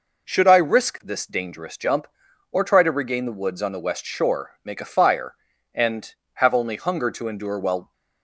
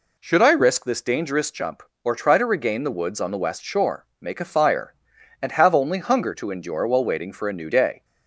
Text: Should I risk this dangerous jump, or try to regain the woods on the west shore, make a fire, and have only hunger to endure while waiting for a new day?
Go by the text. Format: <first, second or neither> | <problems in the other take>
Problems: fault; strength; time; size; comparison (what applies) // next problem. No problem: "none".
second | stops before "waiting for a new day"; at 7.9 s